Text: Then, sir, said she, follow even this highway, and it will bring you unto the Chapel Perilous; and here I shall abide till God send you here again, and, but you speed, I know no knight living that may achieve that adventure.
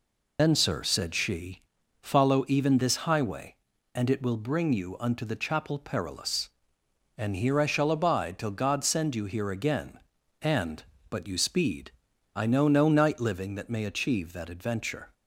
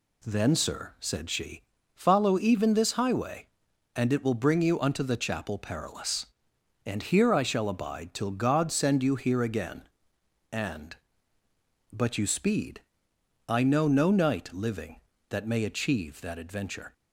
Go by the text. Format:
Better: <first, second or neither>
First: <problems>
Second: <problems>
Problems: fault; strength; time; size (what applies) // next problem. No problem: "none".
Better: second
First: loses the start of "Then"; at 0.3 s; 125 ms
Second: none